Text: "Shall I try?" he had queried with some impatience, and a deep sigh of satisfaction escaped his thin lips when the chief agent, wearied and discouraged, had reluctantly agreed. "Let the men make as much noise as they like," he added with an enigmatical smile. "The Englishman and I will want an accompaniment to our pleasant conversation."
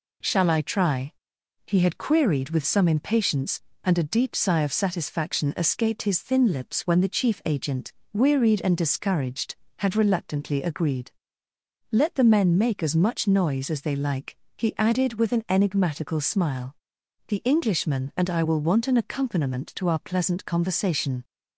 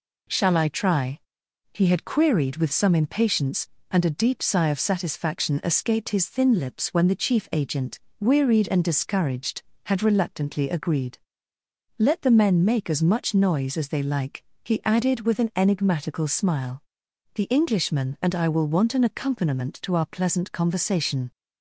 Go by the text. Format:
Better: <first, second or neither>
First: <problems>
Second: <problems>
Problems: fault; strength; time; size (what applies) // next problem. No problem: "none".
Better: neither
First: none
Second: none